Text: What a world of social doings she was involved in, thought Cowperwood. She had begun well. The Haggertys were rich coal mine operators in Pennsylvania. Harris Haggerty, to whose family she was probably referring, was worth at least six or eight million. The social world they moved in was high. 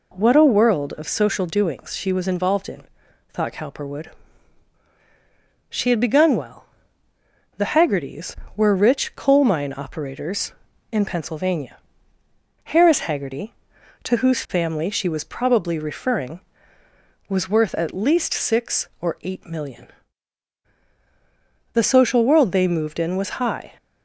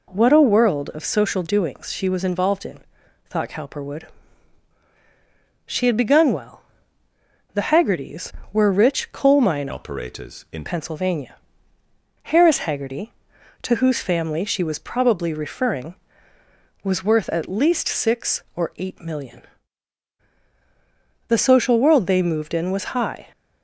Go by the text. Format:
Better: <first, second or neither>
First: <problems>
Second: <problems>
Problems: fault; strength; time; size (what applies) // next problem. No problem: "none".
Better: first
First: none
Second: changes voice from "operators" to "in"; from 9.7 to 10.6 s; 0.9 s long